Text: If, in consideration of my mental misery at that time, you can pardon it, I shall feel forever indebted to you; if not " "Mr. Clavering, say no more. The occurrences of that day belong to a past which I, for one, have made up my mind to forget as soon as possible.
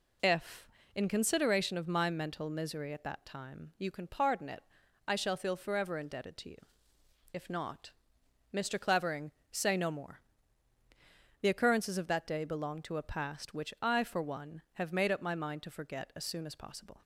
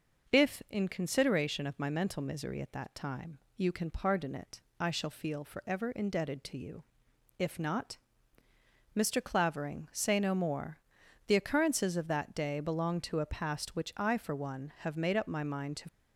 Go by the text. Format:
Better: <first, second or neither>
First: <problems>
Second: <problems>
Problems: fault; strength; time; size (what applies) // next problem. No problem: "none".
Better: first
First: none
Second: starts louder than the rest; until 1.4 s; 6.5 dB // stops before "forget as soon as possible"; at 15.8 s